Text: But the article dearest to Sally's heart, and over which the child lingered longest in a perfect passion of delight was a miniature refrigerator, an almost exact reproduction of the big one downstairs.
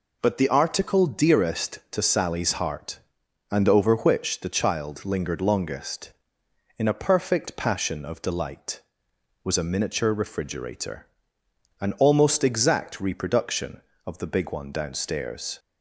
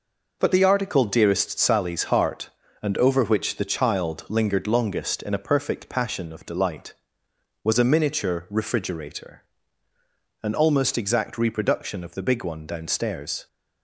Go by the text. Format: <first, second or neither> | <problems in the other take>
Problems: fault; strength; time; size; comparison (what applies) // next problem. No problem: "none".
first | skips "to"; at 1.5 s